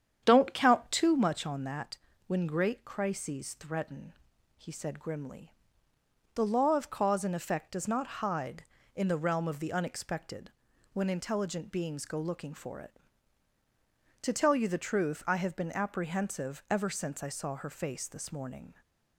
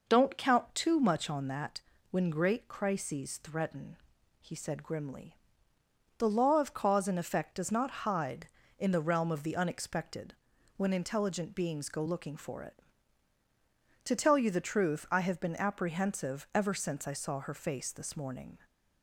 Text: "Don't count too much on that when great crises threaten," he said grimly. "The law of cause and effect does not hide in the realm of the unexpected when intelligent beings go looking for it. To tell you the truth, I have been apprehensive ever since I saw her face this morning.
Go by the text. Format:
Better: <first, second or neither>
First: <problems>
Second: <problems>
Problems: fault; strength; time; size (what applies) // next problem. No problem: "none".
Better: second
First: starts louder than the rest; strong; until 1.2 s; 8.5 dB // pauses between "that" and "when"; slight; at 1.9 s; 0.32 s long // pauses between "unexpected" and "when"; at 10.5 s; 0.42 s long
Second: pauses between "that" and "when"; slight; at 1.8 s; 0.32 s long // pauses between "unexpected" and "when"; at 10.3 s; 0.42 s long